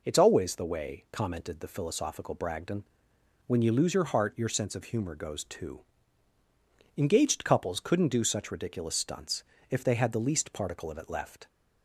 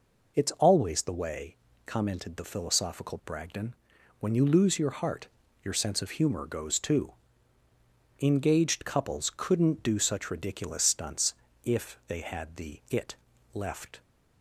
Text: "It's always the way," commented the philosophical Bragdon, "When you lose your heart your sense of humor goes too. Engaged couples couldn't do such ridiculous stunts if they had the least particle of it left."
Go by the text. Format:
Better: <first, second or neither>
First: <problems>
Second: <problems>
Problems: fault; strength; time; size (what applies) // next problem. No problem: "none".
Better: first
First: pauses between "stunts" and "if"; slight; at 9.4 s; 0.24 s long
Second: pauses between "heart" and "your"; slight; at 5.2 s; 0.36 s long // pauses between "stunts" and "if"; slight; at 11.3 s; 0.28 s long // skips "least particle of"; at 12.8 s // pauses between "it" and "left"; at 13.1 s; 0.38 s long